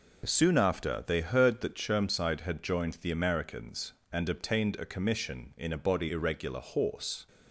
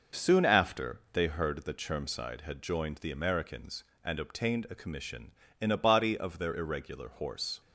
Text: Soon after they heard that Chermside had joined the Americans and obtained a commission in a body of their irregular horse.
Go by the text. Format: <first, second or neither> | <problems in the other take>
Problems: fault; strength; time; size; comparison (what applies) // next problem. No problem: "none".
second | skips "of their"; at 6.0 s